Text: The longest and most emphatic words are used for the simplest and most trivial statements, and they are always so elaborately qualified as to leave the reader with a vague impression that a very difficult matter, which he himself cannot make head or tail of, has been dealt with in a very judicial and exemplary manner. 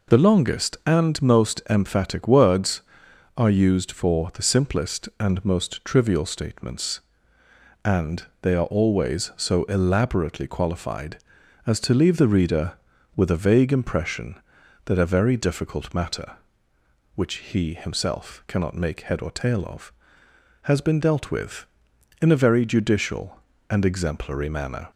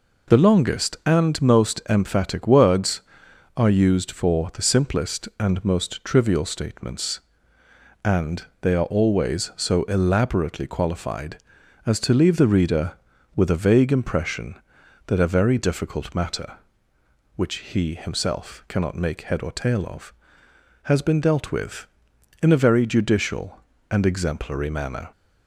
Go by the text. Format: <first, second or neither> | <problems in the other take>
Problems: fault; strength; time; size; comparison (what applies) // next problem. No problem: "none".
neither | pauses between "and" and "they"; slight; the same in both // pauses between "which" and "he"; slight; the same in both